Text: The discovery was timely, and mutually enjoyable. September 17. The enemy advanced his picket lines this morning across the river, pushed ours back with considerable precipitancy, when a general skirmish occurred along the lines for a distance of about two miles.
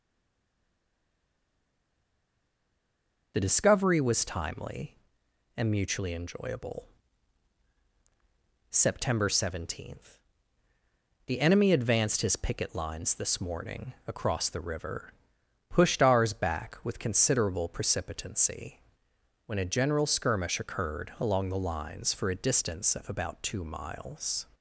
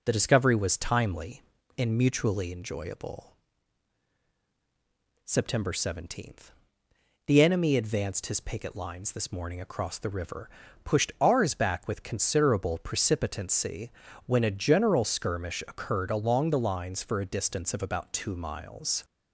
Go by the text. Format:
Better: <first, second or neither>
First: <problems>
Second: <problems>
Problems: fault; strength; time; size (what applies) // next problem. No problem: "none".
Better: second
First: stays silent before the first word; strong; until 3.3 s; 3.3 s long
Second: none